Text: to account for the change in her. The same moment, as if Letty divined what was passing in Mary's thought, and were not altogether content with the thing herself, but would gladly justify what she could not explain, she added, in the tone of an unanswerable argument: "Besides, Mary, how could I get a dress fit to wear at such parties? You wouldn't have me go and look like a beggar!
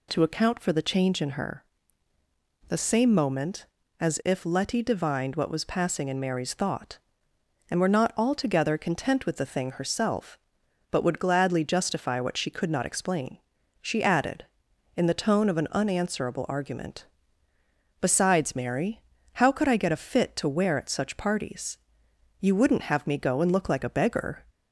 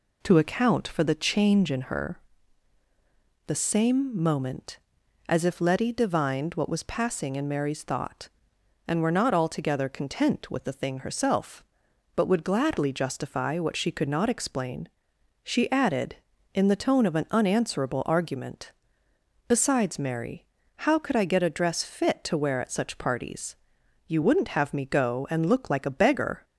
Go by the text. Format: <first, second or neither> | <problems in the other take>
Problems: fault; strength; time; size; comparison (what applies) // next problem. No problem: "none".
second | skips "dress"; at 19.9 s